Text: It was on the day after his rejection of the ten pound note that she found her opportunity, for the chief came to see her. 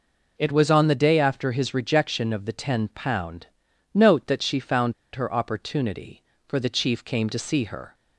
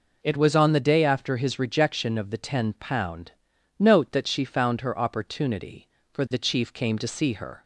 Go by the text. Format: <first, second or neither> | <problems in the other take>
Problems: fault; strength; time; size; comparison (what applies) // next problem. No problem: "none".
second | pauses between "pound" and "note"; noticeable; at 3.4 s; 0.48 s long; noticeable in the second // pauses between "found" and "her"; slight; at 4.9 s; 0.22 s long